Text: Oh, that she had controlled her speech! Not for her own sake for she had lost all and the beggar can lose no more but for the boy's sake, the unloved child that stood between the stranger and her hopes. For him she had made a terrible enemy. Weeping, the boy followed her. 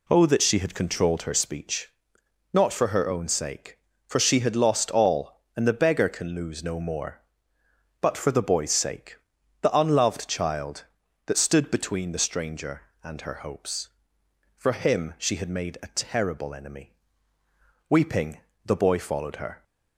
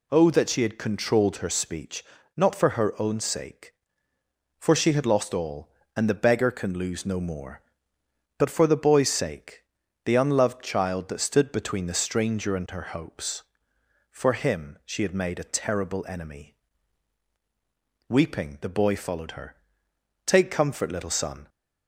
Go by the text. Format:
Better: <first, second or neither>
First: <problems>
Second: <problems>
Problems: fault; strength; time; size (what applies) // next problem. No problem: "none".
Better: first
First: none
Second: goes on to say "Take comfort little son"; noticeable; from 20.2 s on; 1.2 s long